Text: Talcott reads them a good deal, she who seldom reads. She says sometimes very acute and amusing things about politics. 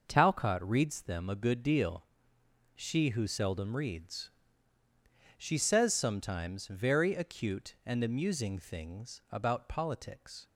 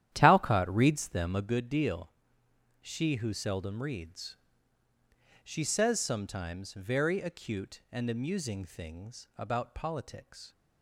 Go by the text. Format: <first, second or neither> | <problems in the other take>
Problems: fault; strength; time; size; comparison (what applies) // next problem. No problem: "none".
first | starts louder than the rest; strong; until 1.5 s; 11 dB